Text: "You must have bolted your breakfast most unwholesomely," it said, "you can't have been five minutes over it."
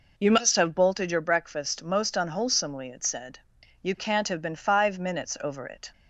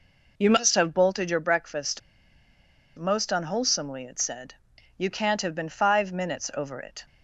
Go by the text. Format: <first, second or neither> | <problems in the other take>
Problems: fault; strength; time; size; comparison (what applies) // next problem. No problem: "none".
first | pauses between "breakfast" and "most"; noticeable; at 1.9 s; 0.97 s long